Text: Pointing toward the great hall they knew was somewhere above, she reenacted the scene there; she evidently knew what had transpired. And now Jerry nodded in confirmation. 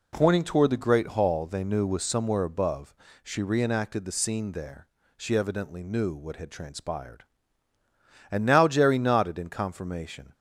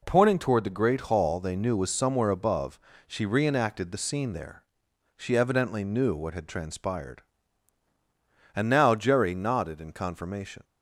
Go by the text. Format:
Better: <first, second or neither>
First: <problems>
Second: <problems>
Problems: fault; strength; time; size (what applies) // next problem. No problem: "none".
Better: neither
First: none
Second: none